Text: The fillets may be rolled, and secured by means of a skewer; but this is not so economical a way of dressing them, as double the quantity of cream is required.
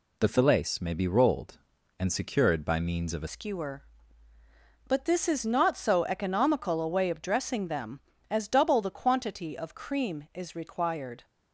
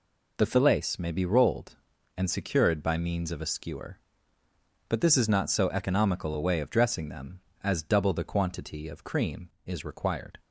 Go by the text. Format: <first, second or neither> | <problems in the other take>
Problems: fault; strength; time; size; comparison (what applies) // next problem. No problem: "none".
second | changes voice at "skewer"; from 3.2 s on; 8.0 s long